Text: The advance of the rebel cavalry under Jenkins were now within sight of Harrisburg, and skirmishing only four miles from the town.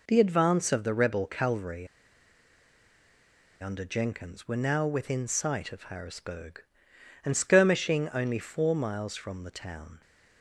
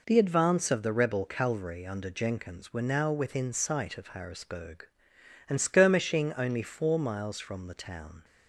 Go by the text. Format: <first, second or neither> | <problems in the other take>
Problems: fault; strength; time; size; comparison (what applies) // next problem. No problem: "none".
second | pauses between "cavalry" and "under"; strong; at 1.8 s; 1.7 s long